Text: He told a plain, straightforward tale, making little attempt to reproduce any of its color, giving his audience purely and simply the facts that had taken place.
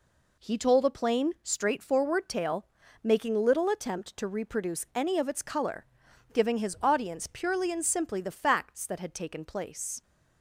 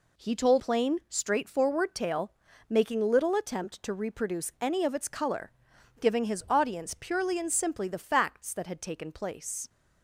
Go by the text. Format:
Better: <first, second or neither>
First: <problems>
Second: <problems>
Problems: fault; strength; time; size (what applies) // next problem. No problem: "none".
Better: first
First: none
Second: skips "a"; at 0.5 s